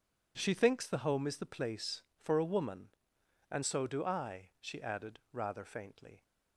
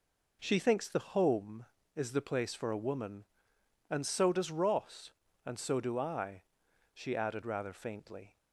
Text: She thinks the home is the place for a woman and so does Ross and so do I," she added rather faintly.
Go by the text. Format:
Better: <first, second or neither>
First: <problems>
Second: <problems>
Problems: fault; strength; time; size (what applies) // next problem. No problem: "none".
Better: second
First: skips "so does Ross and"; at 3.6 s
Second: none